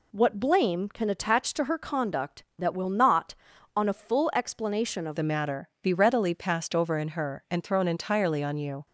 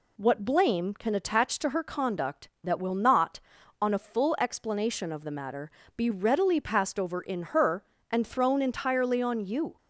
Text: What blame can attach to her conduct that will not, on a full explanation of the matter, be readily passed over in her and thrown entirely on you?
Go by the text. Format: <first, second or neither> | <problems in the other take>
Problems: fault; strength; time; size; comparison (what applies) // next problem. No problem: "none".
second | changes voice at "the"; from 5.1 s on; 3.7 s long